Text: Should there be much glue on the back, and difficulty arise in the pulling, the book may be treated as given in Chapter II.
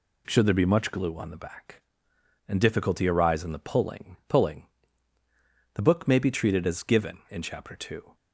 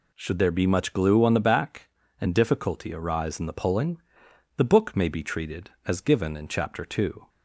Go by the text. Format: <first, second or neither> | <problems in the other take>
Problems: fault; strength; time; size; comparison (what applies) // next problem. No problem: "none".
second | says "pulling" twice; at 4.2 s